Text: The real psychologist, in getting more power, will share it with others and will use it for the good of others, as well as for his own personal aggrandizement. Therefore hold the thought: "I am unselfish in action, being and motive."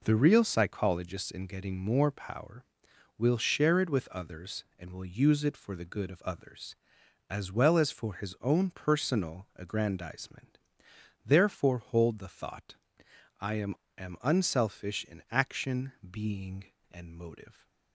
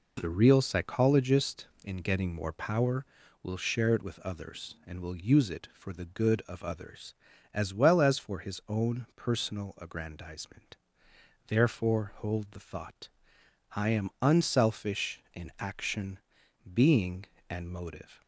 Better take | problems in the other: second | says "am" twice; at 13.9 s

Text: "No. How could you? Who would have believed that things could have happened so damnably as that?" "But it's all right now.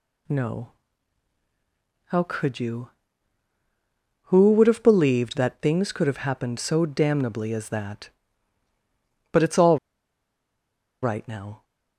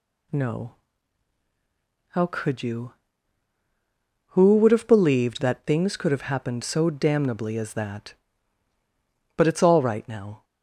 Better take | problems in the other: second | pauses between "all" and "right"; strong; at 9.7 s; 1.2 s long

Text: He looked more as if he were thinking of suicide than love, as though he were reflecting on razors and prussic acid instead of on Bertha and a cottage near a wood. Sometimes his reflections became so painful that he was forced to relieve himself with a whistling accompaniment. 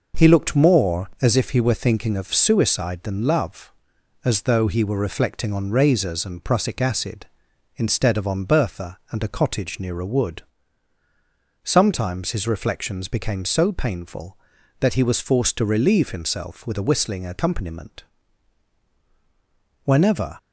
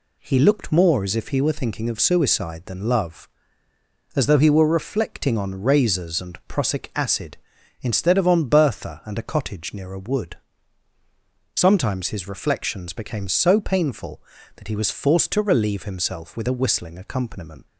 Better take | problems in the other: second | goes on to say "Whenever"; from 19.8 s on; 0.54 s long

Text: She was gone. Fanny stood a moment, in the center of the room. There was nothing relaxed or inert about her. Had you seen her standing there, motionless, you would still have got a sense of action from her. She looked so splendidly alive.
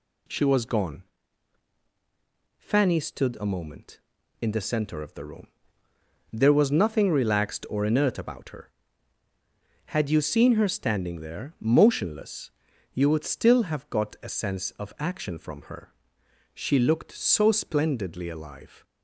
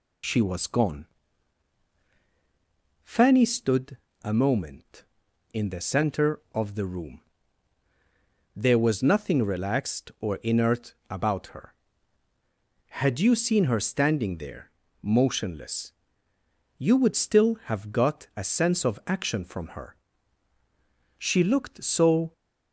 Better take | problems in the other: first | pauses between "stood" and "a"; slight; at 3.9 s; 0.24 s long // pauses between "inert" and "about"; slight; at 10.9 s; 0.16 s long // stops before "splendidly alive"; at 22.3 s

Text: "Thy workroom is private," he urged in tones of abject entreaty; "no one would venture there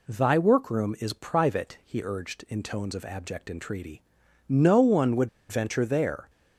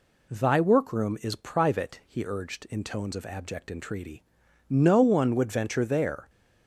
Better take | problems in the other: second | pauses between "would" and "venture"; slight; at 5.2 s; 0.22 s long

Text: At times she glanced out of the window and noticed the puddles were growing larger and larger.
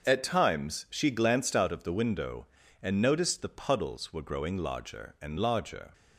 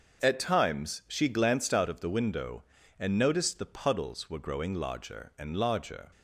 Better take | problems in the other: neither | starts louder than the rest; the same in both

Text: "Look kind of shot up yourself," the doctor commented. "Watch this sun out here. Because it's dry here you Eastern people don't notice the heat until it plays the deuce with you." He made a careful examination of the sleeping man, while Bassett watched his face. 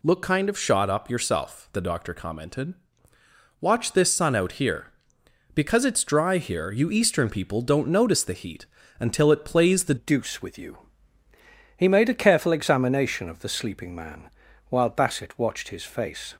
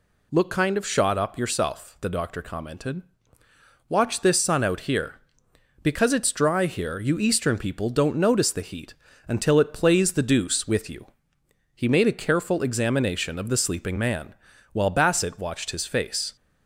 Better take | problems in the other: second | pauses between "heat" and "until"; slight; at 8.6 s; 0.32 s long; slight in the second // changes voice at "deuce"; from 9.9 s on; 6.4 s long

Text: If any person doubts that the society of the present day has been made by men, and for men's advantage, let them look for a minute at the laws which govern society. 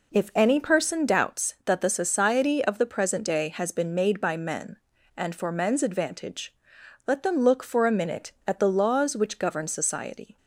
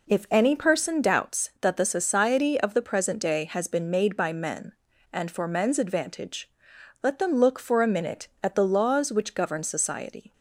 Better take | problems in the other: neither | none

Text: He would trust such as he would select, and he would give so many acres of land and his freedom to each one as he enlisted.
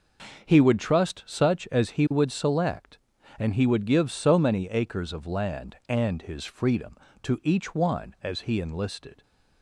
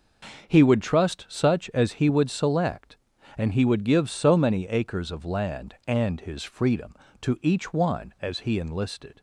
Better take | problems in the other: neither | starts louder than the rest; the same in both

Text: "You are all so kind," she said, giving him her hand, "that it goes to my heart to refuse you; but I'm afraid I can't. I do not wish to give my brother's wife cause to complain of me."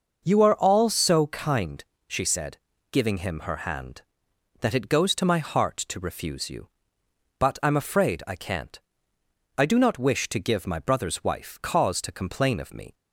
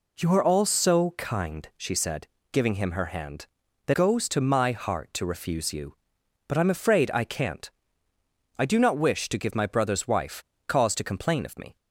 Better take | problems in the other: first | skips "it"; at 3.9 s // pauses between "wife" and "cause"; slight; at 10.4 s; 0.24 s long

